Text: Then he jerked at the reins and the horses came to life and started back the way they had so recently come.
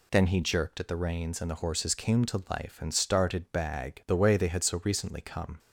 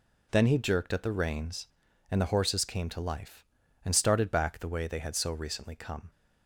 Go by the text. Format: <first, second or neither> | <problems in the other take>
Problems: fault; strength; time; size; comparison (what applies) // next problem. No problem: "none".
second | says "bag" for "back"; at 3.5 s